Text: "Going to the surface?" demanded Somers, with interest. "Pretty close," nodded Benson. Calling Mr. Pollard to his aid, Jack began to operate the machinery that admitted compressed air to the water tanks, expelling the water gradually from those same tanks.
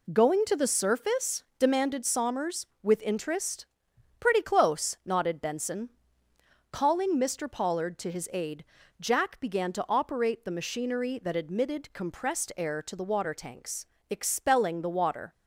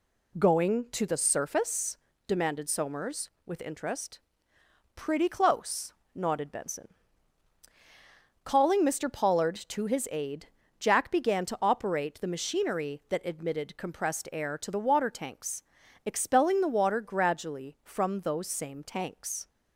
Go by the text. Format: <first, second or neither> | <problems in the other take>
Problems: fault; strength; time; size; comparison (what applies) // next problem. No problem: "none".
second | stops before "gradually from those same tanks"; at 15.3 s